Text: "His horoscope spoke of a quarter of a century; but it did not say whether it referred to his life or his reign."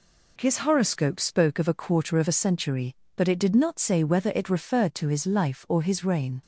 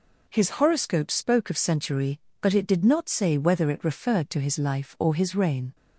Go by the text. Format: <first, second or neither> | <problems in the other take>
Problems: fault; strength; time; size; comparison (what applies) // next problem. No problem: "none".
first | skips "a quarter of a"; at 1.5 s